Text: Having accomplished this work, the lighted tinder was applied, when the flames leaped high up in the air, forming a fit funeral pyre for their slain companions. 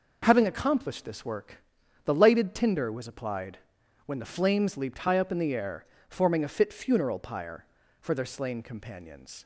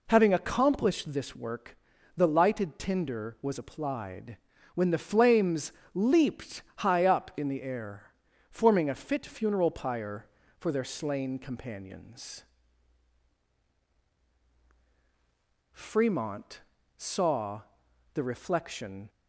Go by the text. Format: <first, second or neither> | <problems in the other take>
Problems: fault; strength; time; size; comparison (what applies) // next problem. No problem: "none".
first | pauses between "flames" and "leaped"; slight; at 5.7 s; 0.22 s long // pauses between "leaped" and "high"; slight; at 6.6 s; 0.16 s long // goes on to say "Fremont saw the reflection"; strong; from 15.7 s on; 3.3 s long